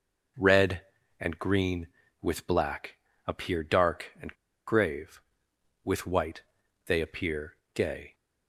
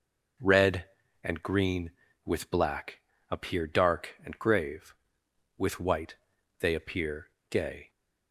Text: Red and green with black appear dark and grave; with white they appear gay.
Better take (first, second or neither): second